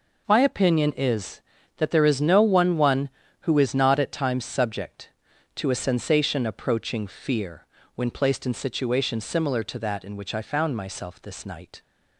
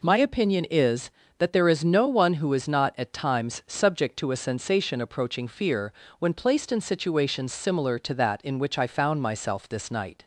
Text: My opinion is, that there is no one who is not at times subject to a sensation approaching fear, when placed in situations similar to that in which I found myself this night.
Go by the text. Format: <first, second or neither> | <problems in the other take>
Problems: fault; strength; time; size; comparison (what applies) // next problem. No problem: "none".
second | says "one" twice; at 2.7 s